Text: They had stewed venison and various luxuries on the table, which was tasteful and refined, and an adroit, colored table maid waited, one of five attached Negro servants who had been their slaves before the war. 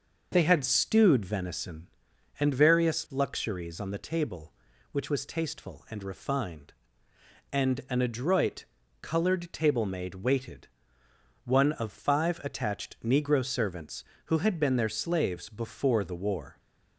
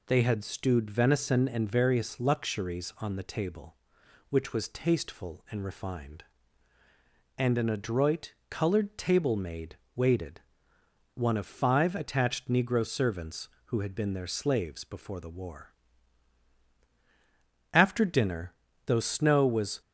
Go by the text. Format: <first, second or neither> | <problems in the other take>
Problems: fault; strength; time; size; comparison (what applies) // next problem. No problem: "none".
first | pauses between "maid" and "waited"; slight; at 9.7 s; 0.18 s long // goes on to say "After dinner though snow was"; strong; from 17.7 s on; 2.0 s long